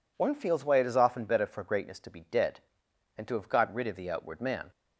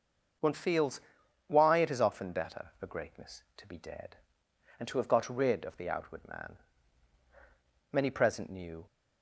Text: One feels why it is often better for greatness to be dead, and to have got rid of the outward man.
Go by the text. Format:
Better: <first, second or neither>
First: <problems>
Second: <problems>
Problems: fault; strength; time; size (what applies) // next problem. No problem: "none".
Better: first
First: none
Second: starts louder than the rest; until 1.8 s; 6.5 dB // pauses between "feels" and "why"; noticeable; at 0.9 s; 0.48 s long // goes on to say "Many present knew"; noticeable; from 7.9 s on; 0.94 s long